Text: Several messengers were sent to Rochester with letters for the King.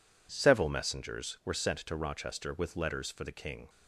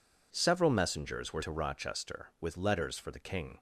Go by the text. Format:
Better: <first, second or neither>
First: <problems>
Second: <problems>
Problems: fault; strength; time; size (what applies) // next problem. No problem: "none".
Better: first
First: none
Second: skips "sent"; at 1.4 s